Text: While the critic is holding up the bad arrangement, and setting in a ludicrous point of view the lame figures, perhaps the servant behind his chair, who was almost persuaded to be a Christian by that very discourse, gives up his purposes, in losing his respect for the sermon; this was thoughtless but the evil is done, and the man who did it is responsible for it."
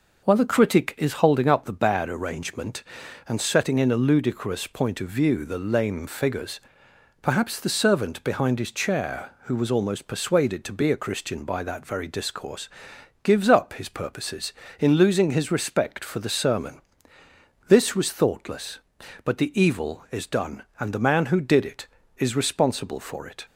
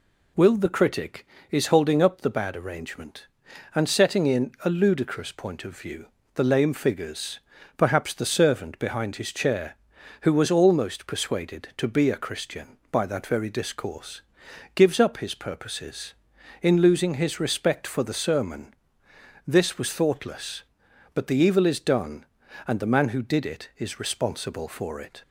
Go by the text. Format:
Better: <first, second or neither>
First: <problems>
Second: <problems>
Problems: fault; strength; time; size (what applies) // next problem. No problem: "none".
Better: first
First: none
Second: says "Will" for "While"; at 0.3 s // pauses between "view" and "the"; slight; at 6.0 s; 0.28 s long